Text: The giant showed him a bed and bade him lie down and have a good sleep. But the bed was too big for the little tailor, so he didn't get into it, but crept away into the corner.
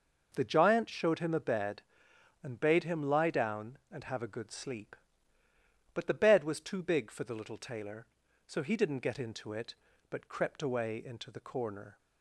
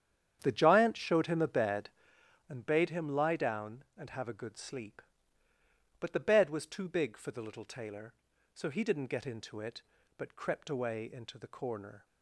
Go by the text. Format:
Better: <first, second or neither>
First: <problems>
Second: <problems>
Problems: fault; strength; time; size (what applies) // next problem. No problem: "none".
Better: first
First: none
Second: starts louder than the rest; strong; until 2.3 s; 9 dB